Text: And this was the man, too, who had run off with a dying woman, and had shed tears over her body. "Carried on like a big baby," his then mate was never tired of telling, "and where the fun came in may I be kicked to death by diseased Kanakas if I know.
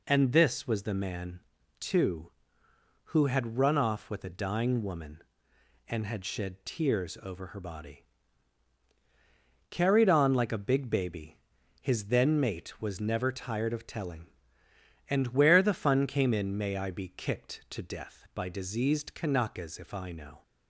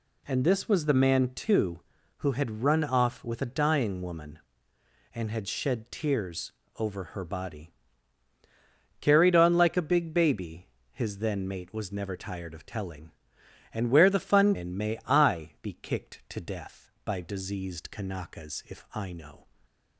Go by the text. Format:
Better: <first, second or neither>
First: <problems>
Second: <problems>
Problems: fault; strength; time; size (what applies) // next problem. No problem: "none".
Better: first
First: none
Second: pauses between "tears" and "over"; slight; at 6.5 s; 0.28 s long // skips "came"; at 14.5 s